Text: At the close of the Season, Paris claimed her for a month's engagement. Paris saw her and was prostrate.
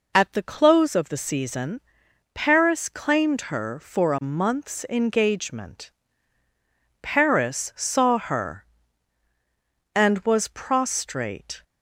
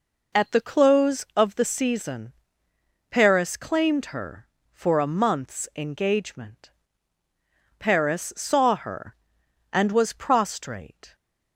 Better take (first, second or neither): neither